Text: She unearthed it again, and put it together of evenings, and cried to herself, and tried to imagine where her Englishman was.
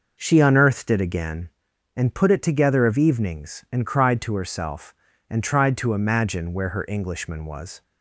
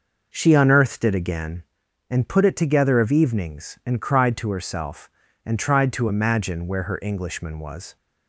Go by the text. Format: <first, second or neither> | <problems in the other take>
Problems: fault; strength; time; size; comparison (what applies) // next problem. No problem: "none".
neither | none